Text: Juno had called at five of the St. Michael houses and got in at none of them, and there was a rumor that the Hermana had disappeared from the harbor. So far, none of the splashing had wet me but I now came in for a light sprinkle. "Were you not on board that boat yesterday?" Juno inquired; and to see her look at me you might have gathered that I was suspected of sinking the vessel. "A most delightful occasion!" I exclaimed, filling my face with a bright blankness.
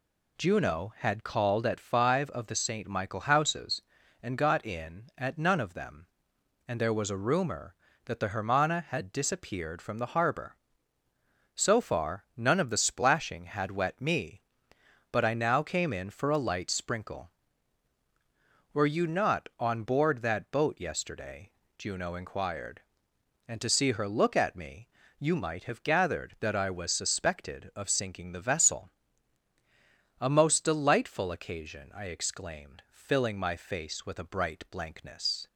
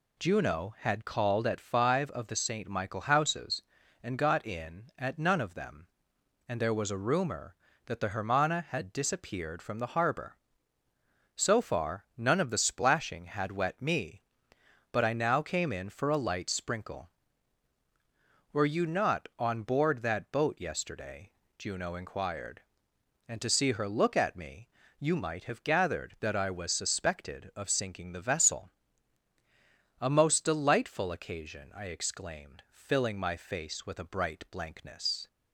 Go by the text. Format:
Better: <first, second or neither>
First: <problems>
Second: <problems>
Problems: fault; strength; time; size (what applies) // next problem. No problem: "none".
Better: neither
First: pauses between "me" and "you"; slight; at 24.8 s; 0.30 s long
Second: pauses between "me" and "you"; slight; at 24.6 s; 0.30 s long